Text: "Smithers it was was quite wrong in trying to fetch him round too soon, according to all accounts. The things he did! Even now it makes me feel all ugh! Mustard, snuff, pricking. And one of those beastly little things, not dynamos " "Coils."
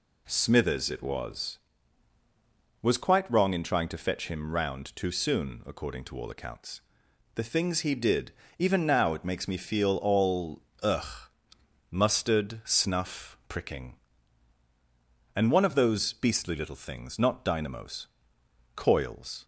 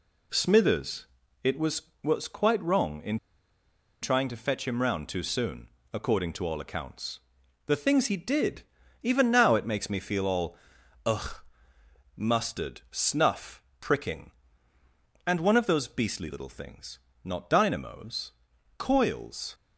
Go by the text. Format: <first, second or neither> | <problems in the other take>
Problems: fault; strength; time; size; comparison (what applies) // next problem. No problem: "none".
first | pauses between "Smithers" and "it"; slight; at 1.0 s; 0.36 s long // pauses between "in" and "trying"; noticeable; at 3.1 s; 0.85 s long // pauses between "all" and "ugh"; noticeable; at 10.5 s; 0.50 s long; slight in the first